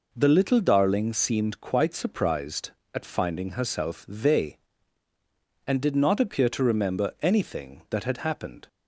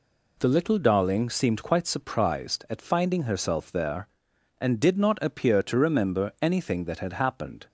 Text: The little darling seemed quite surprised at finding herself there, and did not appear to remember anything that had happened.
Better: second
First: says "they" for "there"; at 4.0 s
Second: none

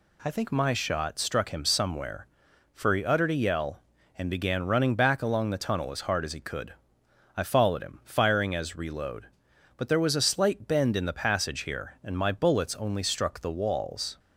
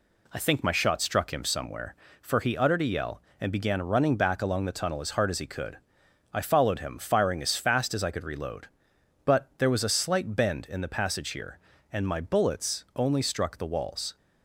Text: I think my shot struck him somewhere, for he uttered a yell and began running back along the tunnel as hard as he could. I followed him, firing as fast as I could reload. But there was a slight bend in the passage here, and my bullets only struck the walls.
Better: second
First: skips "fast as I could"; at 8.7 s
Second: none

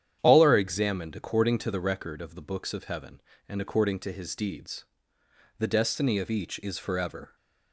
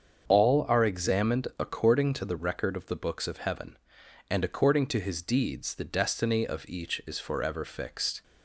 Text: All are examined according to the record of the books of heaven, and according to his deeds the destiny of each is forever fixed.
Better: second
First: starts louder than the rest; strong; until 1.2 s; 9.5 dB // pauses between "deeds" and "the"; noticeable; at 4.8 s; 0.76 s long // stops before "fixed"; at 7.3 s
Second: starts louder than the rest; strong; until 1.3 s; 7 dB

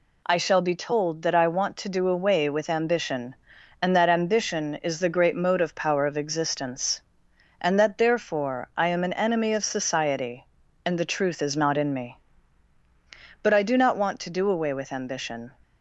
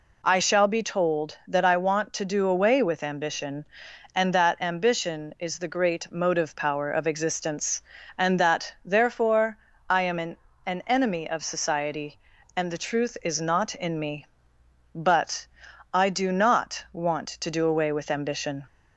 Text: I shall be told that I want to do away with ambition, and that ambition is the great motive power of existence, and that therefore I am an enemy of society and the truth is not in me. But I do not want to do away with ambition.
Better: first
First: none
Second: pauses between "therefore" and "I"; slight; at 9.5 s; 0.32 s long // says "an" twice; at 10.6 s // pauses between "But" and "I"; noticeable; at 15.4 s; 0.48 s long

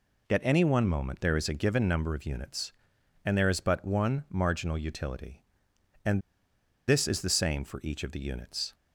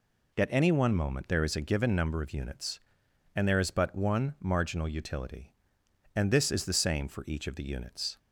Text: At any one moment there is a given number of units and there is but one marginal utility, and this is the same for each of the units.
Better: second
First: pauses between "and" and "this"; noticeable; at 6.2 s; 0.66 s long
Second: none

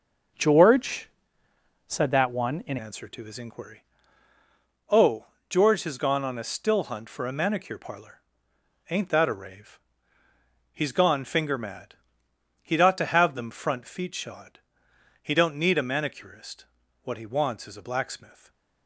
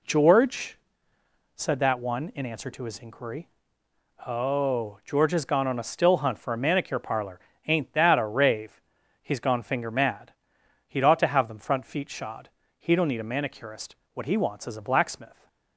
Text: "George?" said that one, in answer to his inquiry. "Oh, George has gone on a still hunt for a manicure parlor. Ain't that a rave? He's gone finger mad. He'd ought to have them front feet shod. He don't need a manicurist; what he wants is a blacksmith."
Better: second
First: changes voice at "answer"; from 2.8 s on; 15.7 s long // stays silent after the last word; slight; from 18.2 s on; 0.6 s long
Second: none

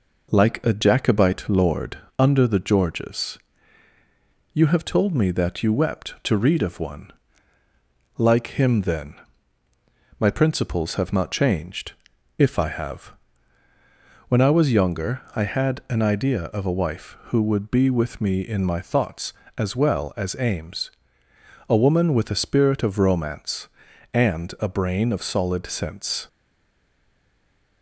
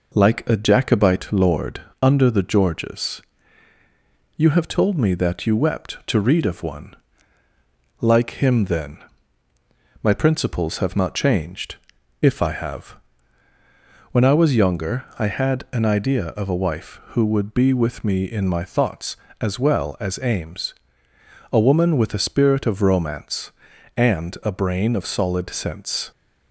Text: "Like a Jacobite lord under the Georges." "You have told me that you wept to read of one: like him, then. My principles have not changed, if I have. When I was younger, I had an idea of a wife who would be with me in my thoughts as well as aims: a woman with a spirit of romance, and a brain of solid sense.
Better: second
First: pauses between "lord" and "under"; slight; at 1.9 s; 0.22 s long // stays silent after the last word; noticeable; from 26.2 s on; 1.6 s long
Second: pauses between "lord" and "under"; slight; at 1.8 s; 0.22 s long

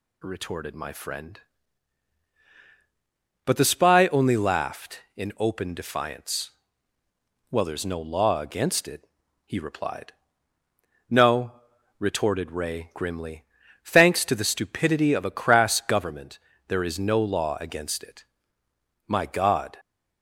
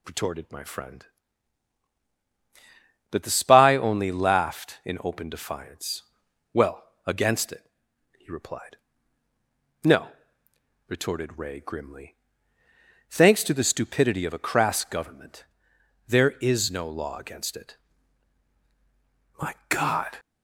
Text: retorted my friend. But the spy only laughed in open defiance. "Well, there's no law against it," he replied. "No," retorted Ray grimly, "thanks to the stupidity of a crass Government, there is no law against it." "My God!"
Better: first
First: none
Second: skips "there's no law"; at 6.9 s

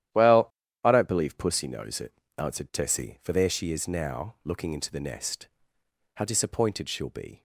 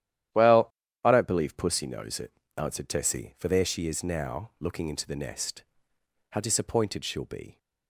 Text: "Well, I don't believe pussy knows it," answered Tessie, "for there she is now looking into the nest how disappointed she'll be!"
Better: neither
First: starts louder than the rest; strong; until 1.4 s; 11.5 dB // pauses between "nest" and "how"; noticeable; at 5.4 s; 0.70 s long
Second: starts louder than the rest; strong; until 1.6 s; 11.5 dB // pauses between "nest" and "how"; noticeable; at 5.6 s; 0.70 s long

